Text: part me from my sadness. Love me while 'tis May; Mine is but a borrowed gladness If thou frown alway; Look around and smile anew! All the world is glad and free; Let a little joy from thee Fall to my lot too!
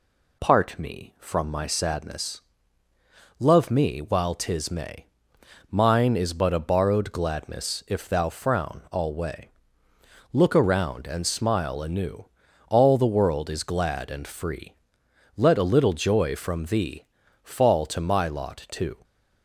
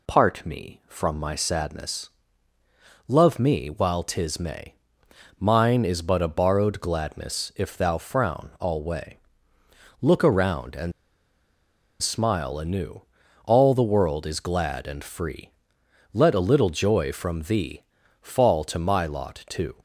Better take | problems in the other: first | pauses between "and" and "smile"; at 10.9 s; 1.0 s long // pauses between "thee" and "Fall"; at 17.8 s; 0.38 s long; also in the first

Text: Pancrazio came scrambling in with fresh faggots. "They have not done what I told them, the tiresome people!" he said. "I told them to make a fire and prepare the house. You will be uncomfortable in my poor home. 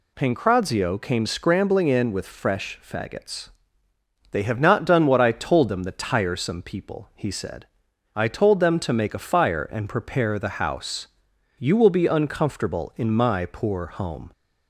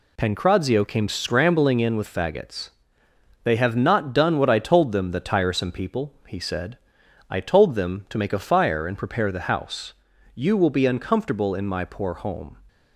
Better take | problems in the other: first | skips "fresh"; at 2.1 s

